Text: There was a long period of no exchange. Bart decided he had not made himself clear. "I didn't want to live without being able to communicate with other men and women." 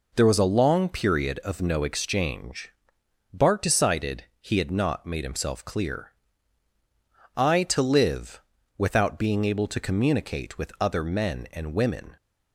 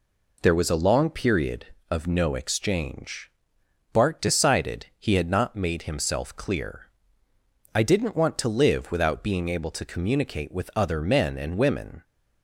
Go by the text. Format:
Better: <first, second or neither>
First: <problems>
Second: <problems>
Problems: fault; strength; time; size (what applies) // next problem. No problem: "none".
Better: second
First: pauses between "decided" and "he"; slight; at 4.2 s; 0.16 s long // skips "didn't want"; at 7.6 s // pauses between "live" and "without"; slight; at 8.4 s; 0.34 s long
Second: none